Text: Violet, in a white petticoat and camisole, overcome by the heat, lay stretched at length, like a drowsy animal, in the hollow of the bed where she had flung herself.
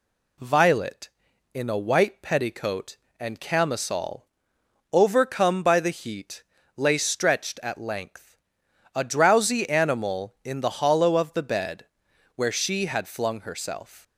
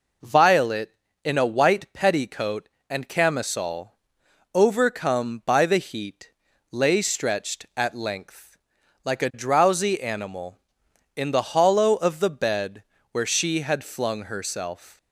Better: second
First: skips "like"; at 8.6 s // pauses between "bed" and "where"; noticeable; at 11.8 s; 0.48 s long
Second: pauses between "bed" and "where"; slight; at 12.8 s; 0.30 s long

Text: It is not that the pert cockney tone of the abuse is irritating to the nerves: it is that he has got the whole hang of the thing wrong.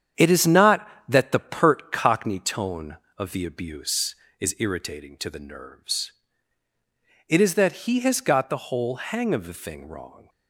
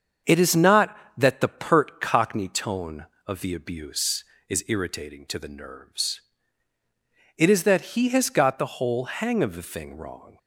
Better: second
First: gets quieter; throughout; 6.5 dB // starts louder than the rest; strong; until 1.3 s; 8.5 dB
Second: starts louder than the rest; strong; until 1.4 s; 7 dB

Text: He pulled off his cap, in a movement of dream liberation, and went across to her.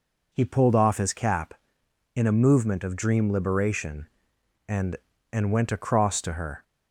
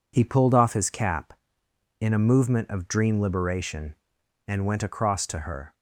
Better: second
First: says "and" twice; at 5.3 s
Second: none

